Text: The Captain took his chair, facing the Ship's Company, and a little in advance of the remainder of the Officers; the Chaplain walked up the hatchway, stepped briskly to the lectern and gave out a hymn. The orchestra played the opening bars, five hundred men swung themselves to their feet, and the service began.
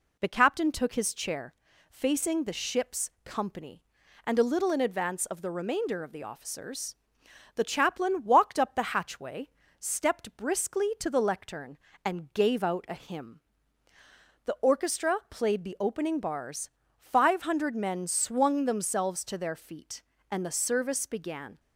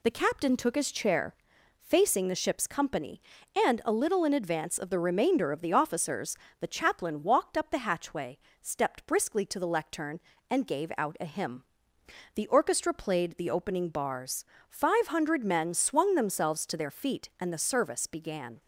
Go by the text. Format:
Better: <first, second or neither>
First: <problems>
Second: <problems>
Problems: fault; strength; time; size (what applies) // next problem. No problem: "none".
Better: neither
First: none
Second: none